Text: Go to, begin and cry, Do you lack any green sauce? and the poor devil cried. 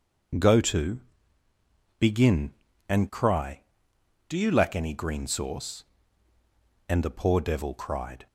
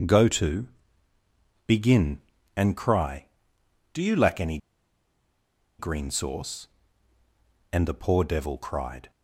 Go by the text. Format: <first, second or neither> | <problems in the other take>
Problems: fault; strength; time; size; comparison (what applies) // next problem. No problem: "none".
first | pauses between "any" and "green"; at 4.5 s; 1.2 s long